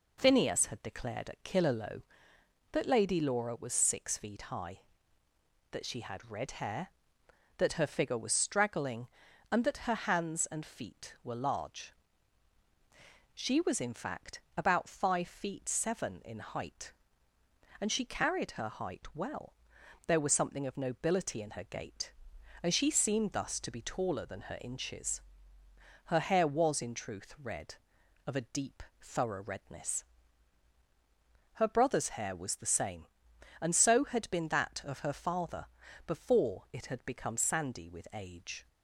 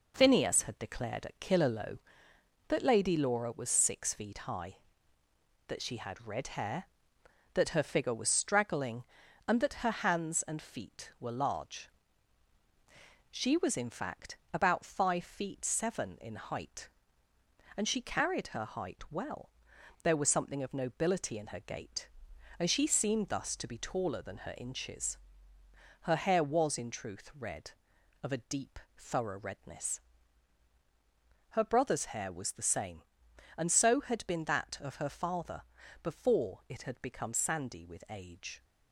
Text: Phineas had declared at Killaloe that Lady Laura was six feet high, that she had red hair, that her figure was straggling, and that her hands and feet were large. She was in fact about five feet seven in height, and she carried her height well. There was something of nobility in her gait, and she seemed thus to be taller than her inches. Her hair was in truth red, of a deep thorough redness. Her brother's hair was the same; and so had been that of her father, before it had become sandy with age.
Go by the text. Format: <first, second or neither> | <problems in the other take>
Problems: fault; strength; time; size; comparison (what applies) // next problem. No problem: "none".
first | gets quieter; noticeable; throughout; 5 dB // pauses between "fact" and "about"; slight; at 14.3 s; 0.16 s long; slight in the first // pauses between "deep" and "thorough"; slight; at 28.7 s; 0.18 s long; slight in the first